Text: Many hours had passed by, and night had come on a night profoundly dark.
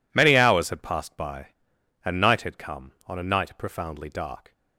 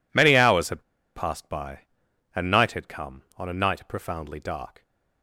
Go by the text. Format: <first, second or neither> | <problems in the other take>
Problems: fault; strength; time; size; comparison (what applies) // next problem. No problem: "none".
first | pauses between "had" and "passed"; slight; at 0.8 s; 0.33 s long